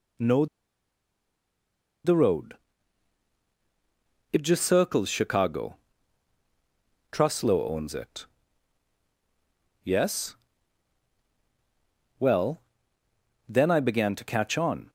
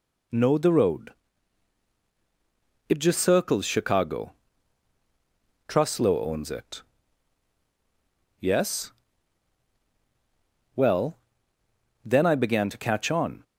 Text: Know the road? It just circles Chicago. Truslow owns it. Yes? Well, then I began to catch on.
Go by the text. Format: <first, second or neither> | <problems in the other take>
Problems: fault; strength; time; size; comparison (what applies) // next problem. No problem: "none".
second | pauses between "Know" and "the"; strong; at 0.4 s; 1.5 s long